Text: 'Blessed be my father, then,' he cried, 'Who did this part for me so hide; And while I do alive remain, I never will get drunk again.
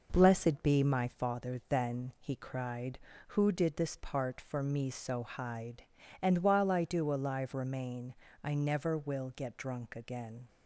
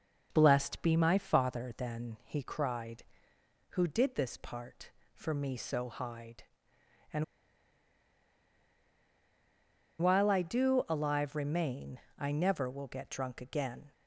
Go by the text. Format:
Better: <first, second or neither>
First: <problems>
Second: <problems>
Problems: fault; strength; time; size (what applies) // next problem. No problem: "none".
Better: first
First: none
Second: pauses between "And" and "while"; strong; at 7.2 s; 2.7 s long